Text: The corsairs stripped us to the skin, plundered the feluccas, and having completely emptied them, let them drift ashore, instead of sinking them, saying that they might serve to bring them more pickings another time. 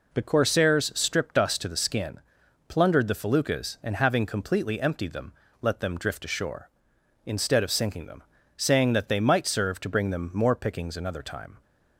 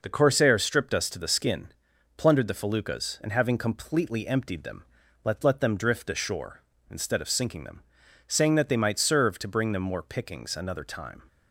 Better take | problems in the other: first | says "let" twice; at 5.4 s

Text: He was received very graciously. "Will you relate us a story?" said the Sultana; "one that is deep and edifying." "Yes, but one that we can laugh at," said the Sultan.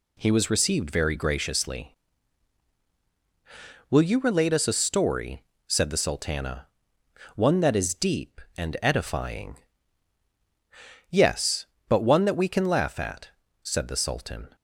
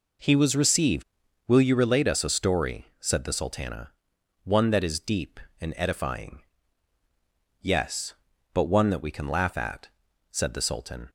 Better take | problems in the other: first | skips "very graciously"; at 1.2 s

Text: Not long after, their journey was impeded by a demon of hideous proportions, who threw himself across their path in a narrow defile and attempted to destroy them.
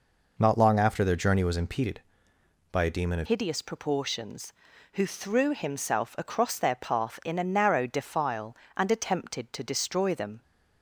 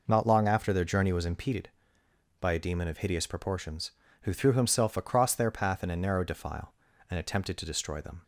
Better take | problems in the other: second | changes voice at "hideous"; from 3.2 s on; 7.2 s long

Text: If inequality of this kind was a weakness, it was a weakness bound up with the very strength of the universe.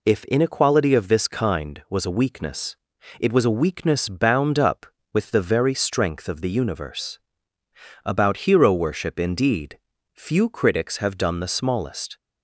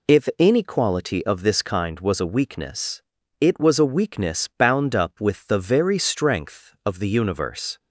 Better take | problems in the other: second | goes on to say "About hero worship indeed few critics have done the smallest"; strong; from 8.0 s on; 4.1 s long

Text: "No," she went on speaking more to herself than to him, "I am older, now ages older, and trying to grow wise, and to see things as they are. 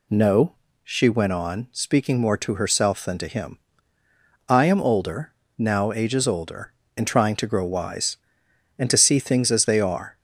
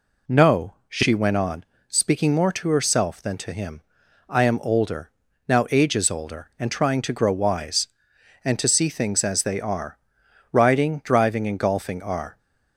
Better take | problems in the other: first | pauses between "on" and "speaking"; slight; at 1.6 s; 0.24 s long // goes on to say "Riding driving and golfing are"; strong; from 10.5 s on; 1.8 s long

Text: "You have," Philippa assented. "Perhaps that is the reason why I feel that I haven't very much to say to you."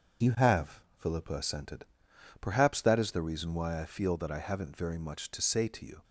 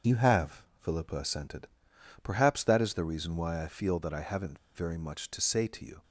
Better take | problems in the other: first | starts louder than the rest; until 1.2 s; 6.5 dB; also in the first // pauses between "haven't" and "very"; slight; at 4.5 s; 0.18 s long

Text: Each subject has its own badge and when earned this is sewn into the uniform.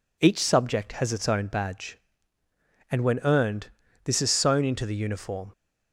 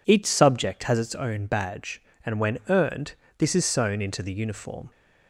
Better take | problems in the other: neither | pauses between "earned" and "this"; slight; the same in both

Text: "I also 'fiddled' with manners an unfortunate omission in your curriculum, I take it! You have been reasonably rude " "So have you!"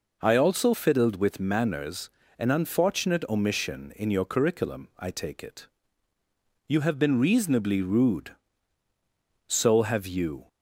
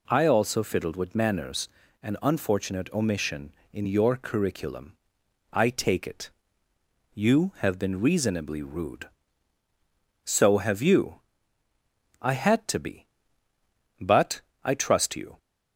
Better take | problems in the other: first | pauses between "manners" and "an"; slight; at 1.6 s; 0.36 s long; slight in the first // goes on to say "I had to be But I trust you"; strong; from 12.1 s on; 3.1 s long

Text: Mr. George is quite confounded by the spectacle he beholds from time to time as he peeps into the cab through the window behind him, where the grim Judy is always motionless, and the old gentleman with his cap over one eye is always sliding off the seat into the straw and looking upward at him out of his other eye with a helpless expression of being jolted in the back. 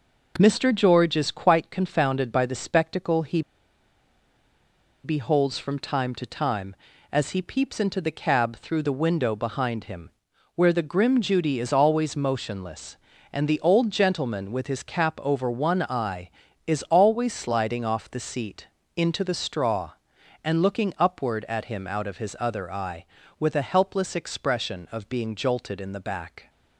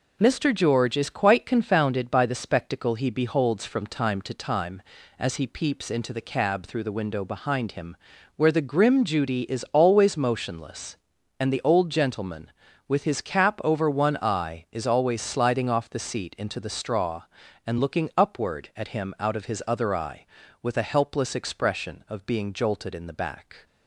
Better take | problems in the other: second | pauses between "he" and "beholds"; strong; at 3.4 s; 1.6 s long // pauses between "seat" and "into"; slight; at 18.6 s; 0.28 s long

